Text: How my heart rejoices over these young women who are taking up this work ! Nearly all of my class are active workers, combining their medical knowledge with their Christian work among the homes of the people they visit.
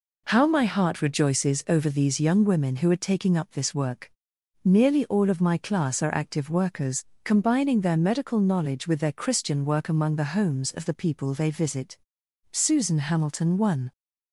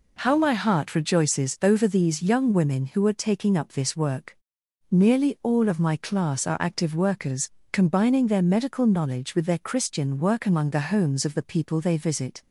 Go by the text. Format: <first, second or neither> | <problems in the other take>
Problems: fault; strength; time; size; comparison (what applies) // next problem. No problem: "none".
second | goes on to say "Susan Hamilton one"; from 12.5 s on; 1.4 s long